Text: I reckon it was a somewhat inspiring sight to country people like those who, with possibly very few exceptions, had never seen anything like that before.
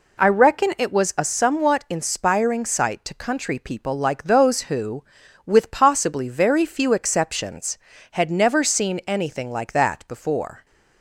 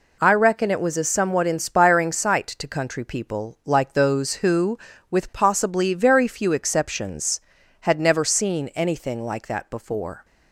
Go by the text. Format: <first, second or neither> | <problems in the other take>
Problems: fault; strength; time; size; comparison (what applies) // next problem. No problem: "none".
neither | none